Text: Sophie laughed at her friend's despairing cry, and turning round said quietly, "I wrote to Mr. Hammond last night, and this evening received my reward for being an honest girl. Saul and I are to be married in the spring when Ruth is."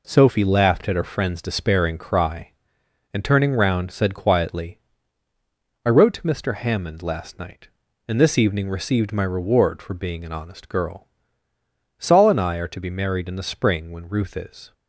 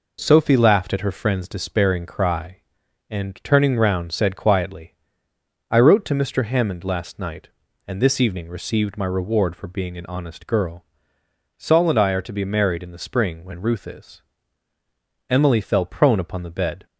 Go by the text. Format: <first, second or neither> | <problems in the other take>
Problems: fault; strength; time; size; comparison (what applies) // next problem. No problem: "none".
first | goes on to say "Emily fell prone upon the bed"; from 15.2 s on; 1.5 s long